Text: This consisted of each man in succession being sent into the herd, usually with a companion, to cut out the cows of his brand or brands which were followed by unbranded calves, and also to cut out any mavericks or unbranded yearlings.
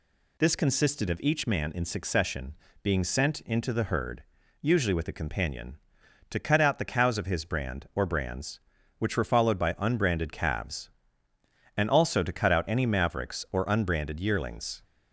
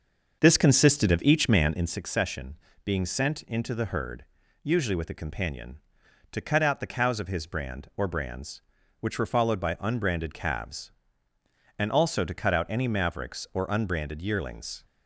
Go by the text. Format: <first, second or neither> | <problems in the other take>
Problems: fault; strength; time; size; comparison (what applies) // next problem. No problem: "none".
first | starts louder than the rest; until 2.0 s; 6 dB // pauses between "succession" and "being"; slight; at 2.5 s; 0.26 s long; slight in the first